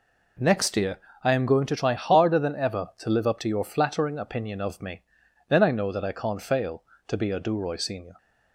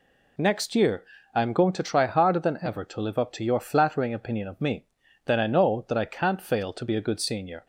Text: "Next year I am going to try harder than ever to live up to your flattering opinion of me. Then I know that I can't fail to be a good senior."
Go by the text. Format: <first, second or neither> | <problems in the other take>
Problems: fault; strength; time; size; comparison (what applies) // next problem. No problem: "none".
second | pauses between "year" and "I"; slight; at 0.9 s; 0.24 s long; slight in the second // says "duroy" for "good"; at 7.3 s